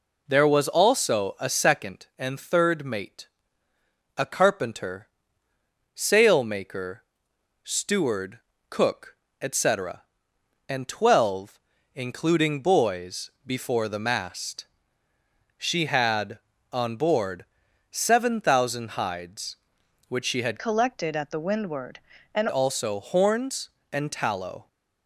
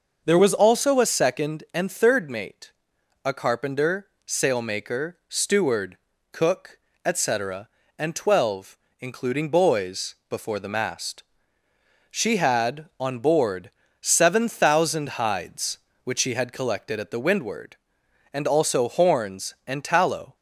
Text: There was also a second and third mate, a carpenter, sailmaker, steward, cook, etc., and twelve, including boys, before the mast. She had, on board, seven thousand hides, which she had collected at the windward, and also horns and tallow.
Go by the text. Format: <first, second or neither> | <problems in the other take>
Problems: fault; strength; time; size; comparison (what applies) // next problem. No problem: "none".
second | changes voice from "collected" to "and"; from 20.5 to 22.4 s; 1.9 s long